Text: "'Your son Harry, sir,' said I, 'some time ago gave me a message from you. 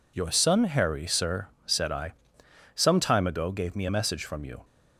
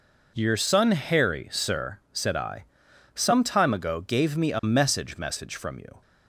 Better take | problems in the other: first | says "message" twice; at 5.1 s

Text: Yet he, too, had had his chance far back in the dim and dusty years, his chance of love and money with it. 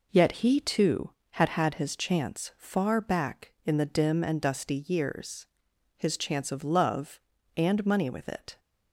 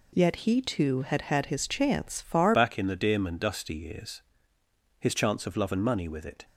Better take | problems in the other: first | changes voice at "back"; from 2.5 s on; 3.9 s long

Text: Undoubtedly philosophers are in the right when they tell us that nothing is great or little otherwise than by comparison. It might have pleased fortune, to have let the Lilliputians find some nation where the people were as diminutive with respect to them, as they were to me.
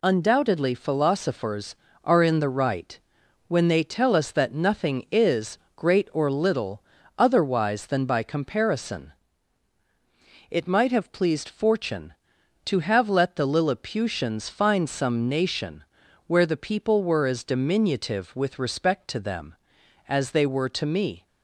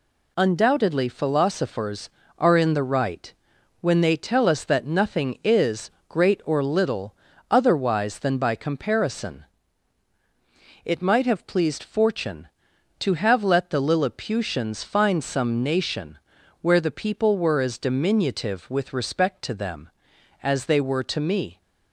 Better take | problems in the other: neither | pauses between "right" and "when"; noticeable; the same in both // pauses between "is" and "great"; slight; the same in both // pauses between "little" and "otherwise"; slight; the same in both // pauses between "nation" and "where"; the same in both

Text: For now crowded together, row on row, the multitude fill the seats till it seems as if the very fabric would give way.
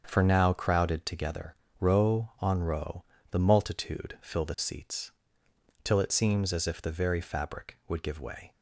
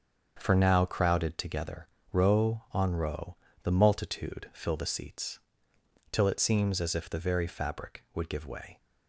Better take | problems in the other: neither | starts louder than the rest; the same in both // pauses between "seats" and "till"; noticeable; the same in both

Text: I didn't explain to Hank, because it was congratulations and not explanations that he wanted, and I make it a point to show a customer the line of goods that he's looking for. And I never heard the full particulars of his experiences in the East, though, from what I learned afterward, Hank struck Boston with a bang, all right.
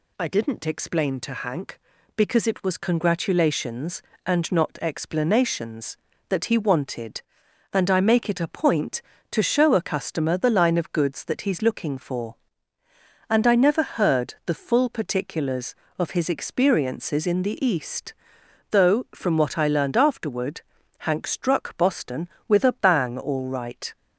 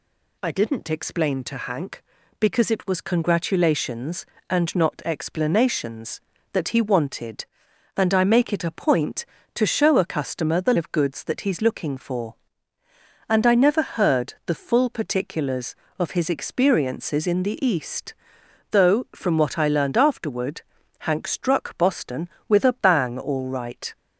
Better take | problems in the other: first | skips "line"; at 10.7 s

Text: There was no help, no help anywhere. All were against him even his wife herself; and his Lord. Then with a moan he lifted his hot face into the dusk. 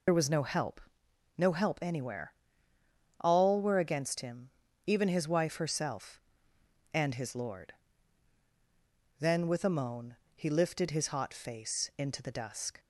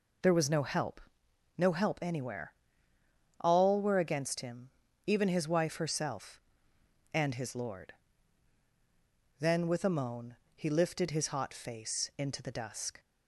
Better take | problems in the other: second | loses the start of "There"; at 0.0 s; 40 ms // pauses between "him" and "even"; at 4.4 s; 0.40 s long; also in the second // pauses between "moan" and "he"; slight; at 10.1 s; 0.18 s long; slight in the second

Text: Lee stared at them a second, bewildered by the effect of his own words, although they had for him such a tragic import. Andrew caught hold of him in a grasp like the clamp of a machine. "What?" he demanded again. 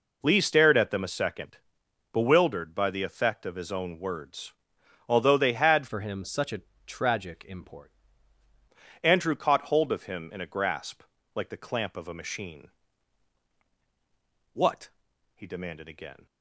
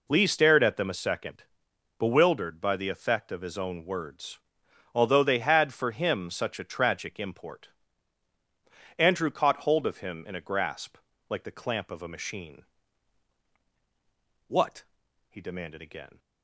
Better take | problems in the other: second | changes voice from "for" to "import"; from 5.8 to 7.9 s; 2.1 s long // pauses between "a" and "tragic"; slight; at 6.6 s; 0.24 s long // pauses between "grasp" and "like"; slight; at 11.0 s; 0.32 s long; slight in the second

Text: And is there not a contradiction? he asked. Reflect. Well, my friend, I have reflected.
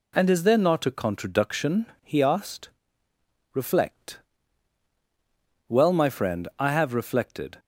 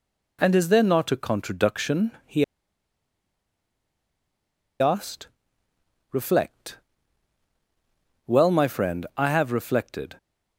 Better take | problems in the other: first | pauses between "he" and "asked"; strong; at 2.4 s; 2.3 s long

